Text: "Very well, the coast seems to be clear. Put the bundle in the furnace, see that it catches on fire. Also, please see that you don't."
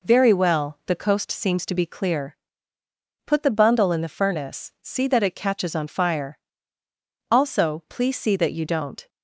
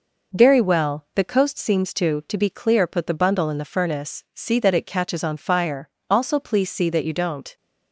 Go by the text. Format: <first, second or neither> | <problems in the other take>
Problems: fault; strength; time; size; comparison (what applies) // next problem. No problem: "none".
first | says "to" twice; at 2.2 s